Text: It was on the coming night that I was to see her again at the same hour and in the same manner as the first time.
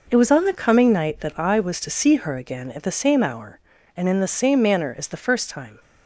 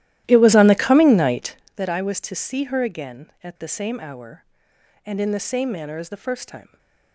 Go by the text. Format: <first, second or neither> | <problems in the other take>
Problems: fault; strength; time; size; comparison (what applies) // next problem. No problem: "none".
first | starts louder than the rest; strong; until 1.7 s; 14 dB